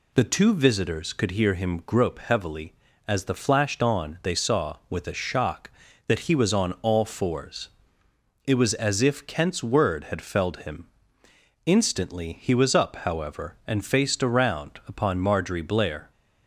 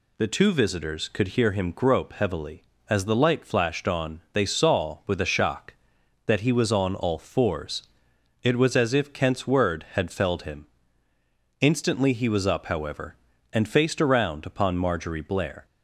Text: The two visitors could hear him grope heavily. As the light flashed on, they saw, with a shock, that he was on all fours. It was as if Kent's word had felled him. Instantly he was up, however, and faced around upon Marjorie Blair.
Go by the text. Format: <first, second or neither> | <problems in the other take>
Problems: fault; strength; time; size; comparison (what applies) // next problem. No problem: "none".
second | skips "light"; at 3.3 s